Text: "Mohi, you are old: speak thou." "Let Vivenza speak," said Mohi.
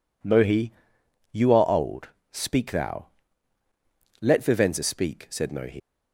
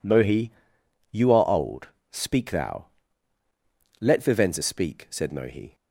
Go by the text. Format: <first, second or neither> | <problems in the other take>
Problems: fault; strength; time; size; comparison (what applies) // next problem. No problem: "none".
second | leaves "Mohi" unfinished; at 5.7 s; 140 ms